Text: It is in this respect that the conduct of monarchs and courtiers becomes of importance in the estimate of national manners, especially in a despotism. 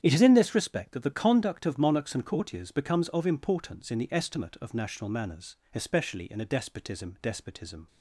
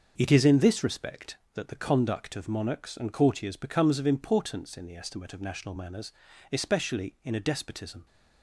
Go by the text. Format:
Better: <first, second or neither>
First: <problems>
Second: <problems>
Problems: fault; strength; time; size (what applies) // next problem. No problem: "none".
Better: second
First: starts louder than the rest; strong; until 1.0 s; 9 dB // says "despotism" twice; at 7.2 s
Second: starts louder than the rest; until 1.1 s; 6 dB